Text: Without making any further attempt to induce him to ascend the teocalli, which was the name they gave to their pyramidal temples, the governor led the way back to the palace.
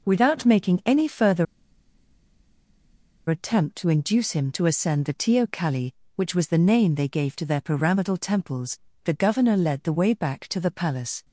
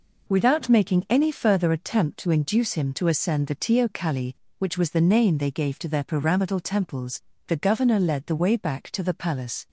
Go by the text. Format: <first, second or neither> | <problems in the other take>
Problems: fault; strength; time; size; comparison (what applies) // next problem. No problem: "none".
second | pauses between "further" and "attempt"; strong; at 1.4 s; 1.8 s long